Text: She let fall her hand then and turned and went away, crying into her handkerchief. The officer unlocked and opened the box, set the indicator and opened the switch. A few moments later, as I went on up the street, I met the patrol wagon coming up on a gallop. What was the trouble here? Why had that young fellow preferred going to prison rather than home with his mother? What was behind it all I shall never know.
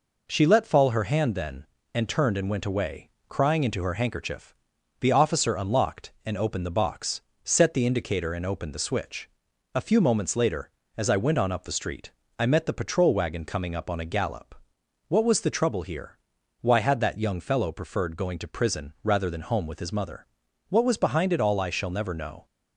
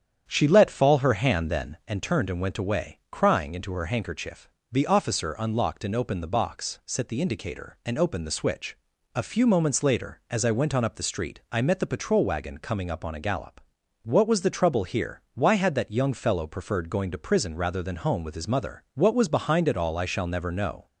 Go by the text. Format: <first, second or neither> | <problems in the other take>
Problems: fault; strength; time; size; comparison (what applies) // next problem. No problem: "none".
first | starts louder than the rest; strong; until 2.0 s; 8.5 dB